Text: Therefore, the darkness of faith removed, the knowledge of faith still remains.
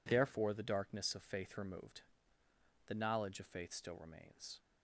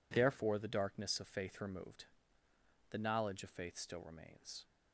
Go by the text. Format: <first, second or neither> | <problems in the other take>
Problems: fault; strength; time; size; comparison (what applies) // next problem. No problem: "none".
neither | none